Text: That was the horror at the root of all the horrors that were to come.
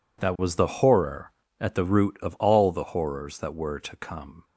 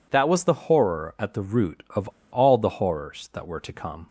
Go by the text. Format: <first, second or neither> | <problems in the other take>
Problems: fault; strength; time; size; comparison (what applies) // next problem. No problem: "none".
first | pauses between "of" and "all"; slight; at 2.0 s; 0.25 s long